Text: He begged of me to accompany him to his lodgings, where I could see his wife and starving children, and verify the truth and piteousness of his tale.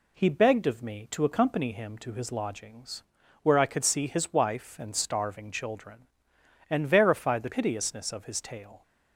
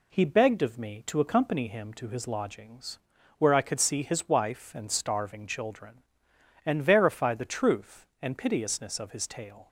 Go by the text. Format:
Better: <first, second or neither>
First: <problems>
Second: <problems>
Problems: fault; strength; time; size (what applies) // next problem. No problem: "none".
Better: second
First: skips "truth and"; at 7.5 s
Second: none